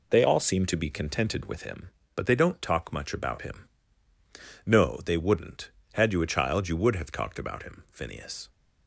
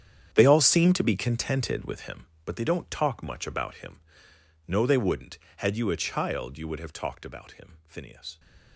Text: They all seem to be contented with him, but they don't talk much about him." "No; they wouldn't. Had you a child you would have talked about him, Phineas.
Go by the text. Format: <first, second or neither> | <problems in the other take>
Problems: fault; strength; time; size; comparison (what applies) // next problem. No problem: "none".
first | gets quieter; strong; throughout; 15 dB